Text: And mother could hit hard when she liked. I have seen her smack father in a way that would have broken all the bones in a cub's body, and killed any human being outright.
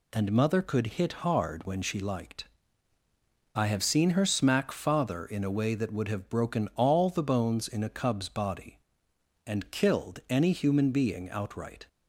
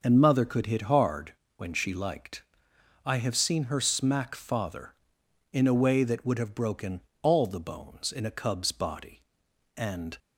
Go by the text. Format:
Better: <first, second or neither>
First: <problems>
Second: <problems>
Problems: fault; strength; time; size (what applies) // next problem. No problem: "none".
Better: first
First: none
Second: starts louder than the rest; until 1.0 s; 6 dB // pauses between "hard" and "when"; slight; at 1.3 s; 0.24 s long // pauses between "broken" and "all"; slight; at 7.0 s; 0.20 s long // stops before "killed any human being outright"; at 10.1 s